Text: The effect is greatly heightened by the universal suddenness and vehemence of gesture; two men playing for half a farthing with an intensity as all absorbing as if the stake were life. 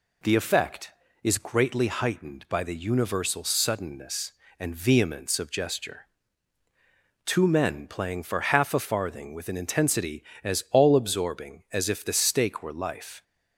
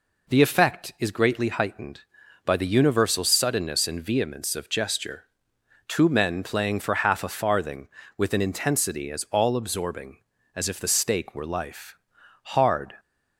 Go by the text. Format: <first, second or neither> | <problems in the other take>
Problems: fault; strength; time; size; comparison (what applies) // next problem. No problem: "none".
first | goes on to say "Hard"; from 12.4 s on; 0.52 s long